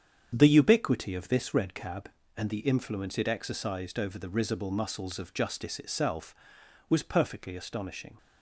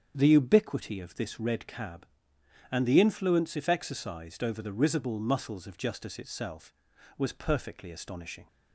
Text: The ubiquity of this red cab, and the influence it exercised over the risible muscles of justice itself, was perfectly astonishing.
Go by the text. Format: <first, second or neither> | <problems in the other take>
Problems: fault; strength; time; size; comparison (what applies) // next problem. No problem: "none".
first | starts louder than the rest; strong; until 1.1 s; 7.5 dB; strong in the first // says "if" for "it"; at 3.5 s